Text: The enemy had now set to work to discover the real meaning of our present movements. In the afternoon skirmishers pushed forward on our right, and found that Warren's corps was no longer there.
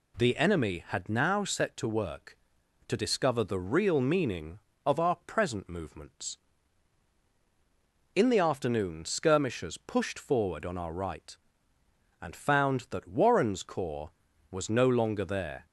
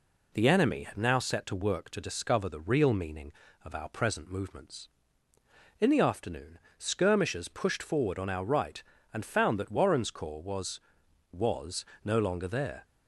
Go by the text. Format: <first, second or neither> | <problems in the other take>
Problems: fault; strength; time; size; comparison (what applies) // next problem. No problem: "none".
first | pauses between "afternoon" and "skirmishers"; slight; at 6.5 s; 0.18 s long // says "was" twice; at 11.3 s